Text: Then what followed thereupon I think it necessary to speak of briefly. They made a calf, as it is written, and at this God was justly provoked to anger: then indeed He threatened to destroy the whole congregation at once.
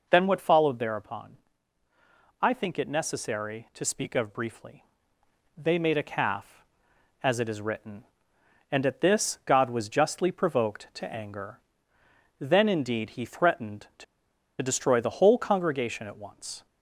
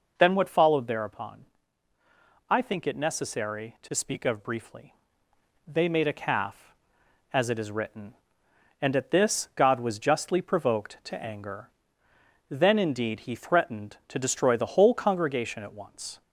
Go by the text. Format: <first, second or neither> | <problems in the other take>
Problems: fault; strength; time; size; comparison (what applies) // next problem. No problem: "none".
second | pauses between "thereupon" and "I"; at 1.3 s; 1.0 s long; also in the second // pauses between "to" and "destroy"; noticeable; at 14.0 s; 0.56 s long